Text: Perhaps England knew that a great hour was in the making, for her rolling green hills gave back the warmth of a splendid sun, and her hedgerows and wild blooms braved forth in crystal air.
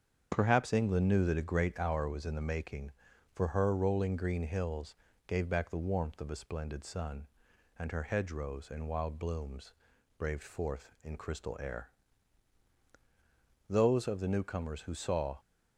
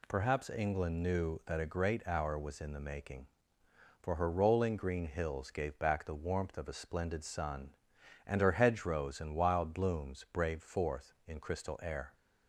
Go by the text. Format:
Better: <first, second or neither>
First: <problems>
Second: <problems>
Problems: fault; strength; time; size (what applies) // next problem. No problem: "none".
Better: second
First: starts louder than the rest; strong; until 1.3 s; 7.5 dB // pauses between "hills" and "gave"; slight; at 4.9 s; 0.32 s long // pauses between "blooms" and "braved"; at 9.7 s; 0.44 s long // goes on to say "Those of the newcomers who saw"; strong; from 13.6 s on; 1.6 s long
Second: none